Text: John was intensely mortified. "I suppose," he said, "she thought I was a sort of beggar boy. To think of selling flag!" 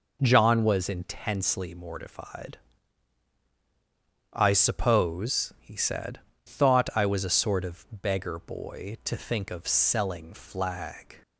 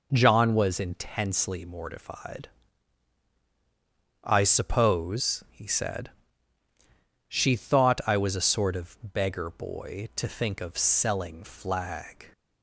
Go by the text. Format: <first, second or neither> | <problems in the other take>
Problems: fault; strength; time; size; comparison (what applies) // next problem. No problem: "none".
second | skips "she"; at 6.3 s